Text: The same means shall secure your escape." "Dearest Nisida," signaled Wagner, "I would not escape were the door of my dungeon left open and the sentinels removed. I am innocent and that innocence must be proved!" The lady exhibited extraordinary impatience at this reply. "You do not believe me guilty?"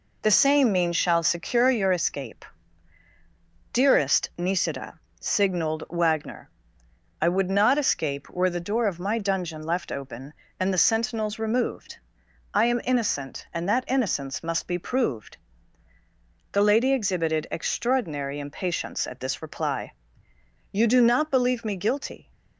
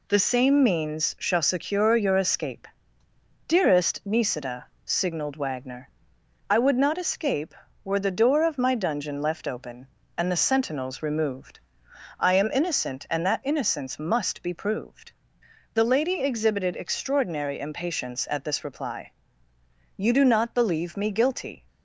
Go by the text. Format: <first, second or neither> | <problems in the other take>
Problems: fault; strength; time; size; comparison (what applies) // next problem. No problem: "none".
neither | none